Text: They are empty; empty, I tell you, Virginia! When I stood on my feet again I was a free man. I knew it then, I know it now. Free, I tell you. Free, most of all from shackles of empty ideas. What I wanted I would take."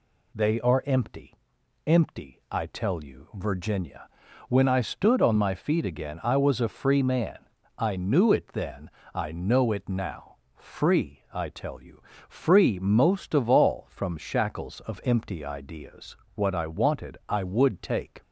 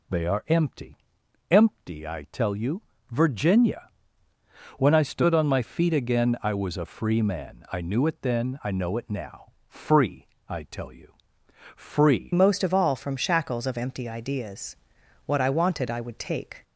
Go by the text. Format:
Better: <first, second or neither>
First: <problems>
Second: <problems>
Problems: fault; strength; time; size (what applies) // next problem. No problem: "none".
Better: first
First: none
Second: changes voice at "most"; from 12.3 s on; 4.3 s long